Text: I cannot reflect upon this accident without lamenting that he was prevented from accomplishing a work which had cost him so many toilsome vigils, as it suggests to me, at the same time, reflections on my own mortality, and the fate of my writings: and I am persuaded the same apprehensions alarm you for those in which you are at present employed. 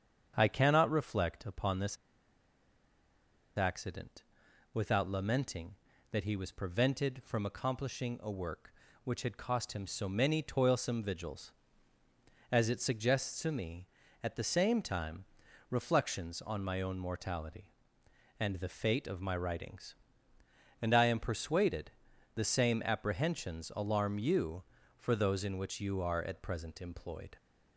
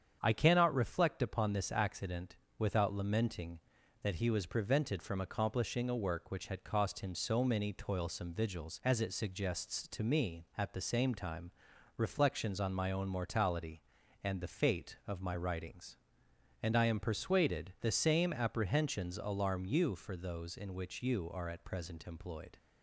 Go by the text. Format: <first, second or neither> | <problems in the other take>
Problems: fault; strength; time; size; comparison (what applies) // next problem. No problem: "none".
second | starts louder than the rest; strong; until 1.3 s; 7.5 dB; strong in the second // pauses between "this" and "accident"; strong; at 1.9 s; 1.5 s long // pauses between "accident" and "without"; noticeable; at 4.2 s; 0.48 s long; slight in the second // pauses between "persuaded" and "the"; at 21.9 s; 0.42 s long